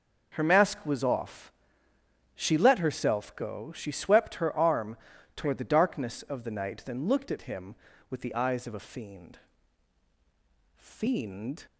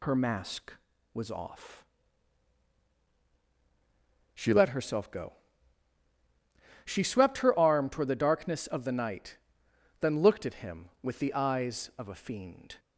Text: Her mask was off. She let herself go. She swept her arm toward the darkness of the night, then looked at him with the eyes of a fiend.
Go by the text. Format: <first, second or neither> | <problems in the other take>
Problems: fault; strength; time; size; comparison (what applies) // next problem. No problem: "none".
second | starts louder than the rest; noticeable; until 1.3 s; 6 dB // pauses between "arm" and "toward"; at 4.9 s; 0.38 s long // says "fiend" twice; at 10.7 s